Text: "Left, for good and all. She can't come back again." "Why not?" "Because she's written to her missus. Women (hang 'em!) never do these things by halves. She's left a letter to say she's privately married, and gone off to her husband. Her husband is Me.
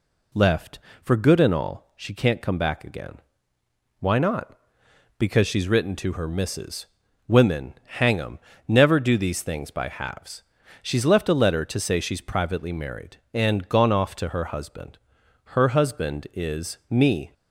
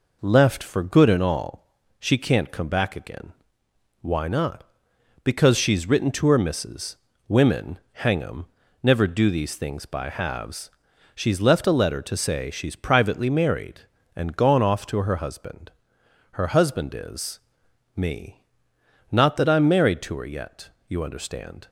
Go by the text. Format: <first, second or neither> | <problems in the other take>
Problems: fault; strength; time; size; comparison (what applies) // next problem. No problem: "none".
first | pauses between "is" and "Me"; noticeable; at 17.3 s; 0.56 s long // goes on to say "Not that I'm married to her yet you understand"; strong; from 19.1 s on; 2.5 s long